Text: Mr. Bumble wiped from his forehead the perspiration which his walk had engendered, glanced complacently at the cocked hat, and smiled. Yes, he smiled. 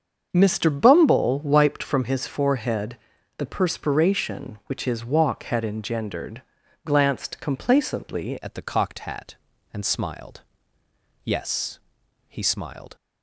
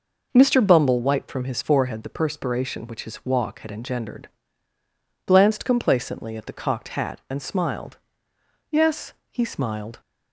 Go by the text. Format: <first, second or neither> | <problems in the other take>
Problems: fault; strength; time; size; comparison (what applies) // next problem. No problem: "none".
second | starts louder than the rest; until 1.3 s; 7 dB // pauses between "forehead" and "the"; at 2.9 s; 0.42 s long // changes voice at "at"; from 8.4 s on; 4.5 s long